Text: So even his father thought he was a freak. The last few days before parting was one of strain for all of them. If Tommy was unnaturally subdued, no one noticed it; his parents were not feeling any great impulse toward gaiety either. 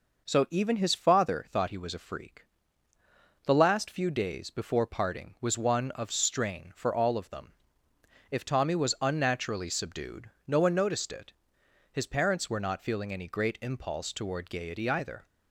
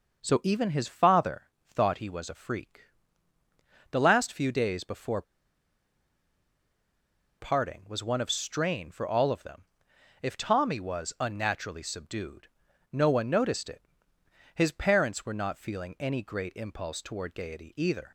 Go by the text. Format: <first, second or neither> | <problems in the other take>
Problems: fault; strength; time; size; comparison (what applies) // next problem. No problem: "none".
first | starts louder than the rest; noticeable; until 1.2 s; 6 dB // pauses between "father" and "thought"; slight; at 1.4 s; 0.30 s long // pauses between "before" and "parting"; strong; at 5.2 s; 2.1 s long